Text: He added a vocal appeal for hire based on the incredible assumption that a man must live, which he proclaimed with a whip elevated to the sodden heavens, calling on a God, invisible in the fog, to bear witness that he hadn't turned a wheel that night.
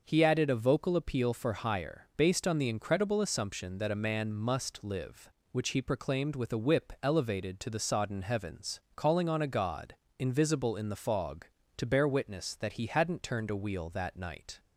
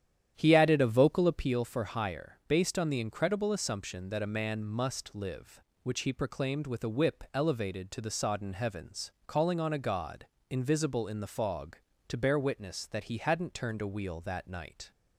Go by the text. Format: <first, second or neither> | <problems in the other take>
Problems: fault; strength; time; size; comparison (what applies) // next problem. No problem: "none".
first | starts louder than the rest; strong; until 1.5 s; 10 dB